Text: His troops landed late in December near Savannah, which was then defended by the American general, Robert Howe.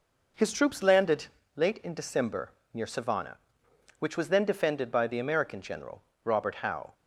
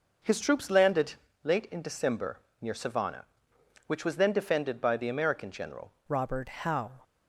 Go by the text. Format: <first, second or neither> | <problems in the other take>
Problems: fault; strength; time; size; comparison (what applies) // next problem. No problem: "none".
first | pauses between "landed" and "late"; slight; at 1.1 s; 0.28 s long; slight in the first // pauses between "December" and "near"; slight; at 2.3 s; 0.22 s long; slight in the first // changes voice at "Robert"; from 6.0 s on; 1.0 s long